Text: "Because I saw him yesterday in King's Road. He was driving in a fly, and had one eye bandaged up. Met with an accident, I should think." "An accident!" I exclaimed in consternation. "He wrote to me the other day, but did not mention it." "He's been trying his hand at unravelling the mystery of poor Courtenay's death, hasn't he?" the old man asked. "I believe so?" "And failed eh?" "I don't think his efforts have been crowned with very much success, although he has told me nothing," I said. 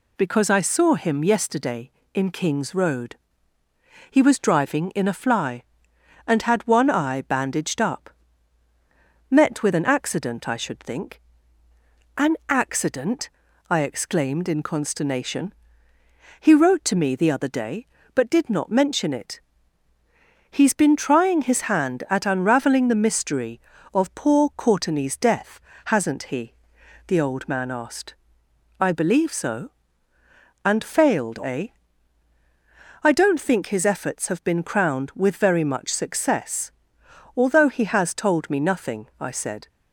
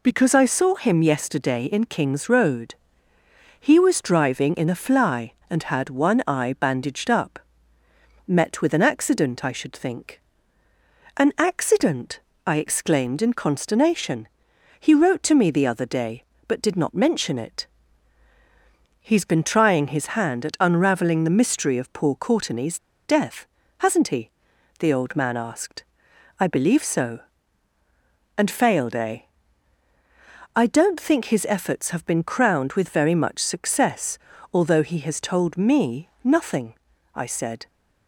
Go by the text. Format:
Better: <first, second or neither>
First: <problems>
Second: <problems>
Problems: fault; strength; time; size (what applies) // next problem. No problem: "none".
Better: first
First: none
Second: pauses between "Courtenay's" and "death"; slight; at 22.7 s; 0.27 s long // pauses between "me" and "nothing"; slight; at 36.0 s; 0.16 s long